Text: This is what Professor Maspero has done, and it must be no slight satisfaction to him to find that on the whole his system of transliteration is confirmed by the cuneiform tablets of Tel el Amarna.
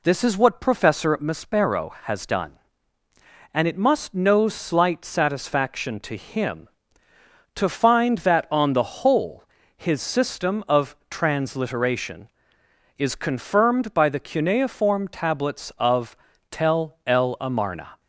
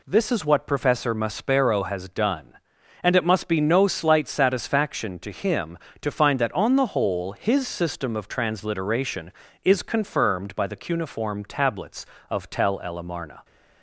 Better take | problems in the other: second | skips "be"; at 4.1 s // pauses between "whole" and "his"; slight; at 9.4 s; 0.32 s long // pauses between "of" and "Tel"; slight; at 16.1 s; 0.34 s long

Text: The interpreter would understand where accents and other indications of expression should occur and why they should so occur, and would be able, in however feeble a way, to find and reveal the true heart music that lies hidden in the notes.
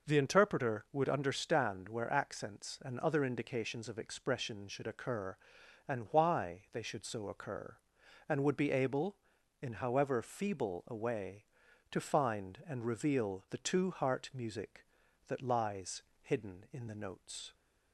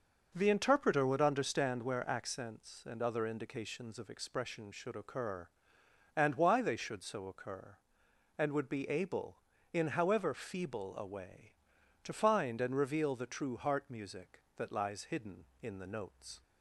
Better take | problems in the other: second | says "two" for "true"; at 13.5 s // pauses between "lies" and "hidden"; slight; at 16.0 s; 0.20 s long

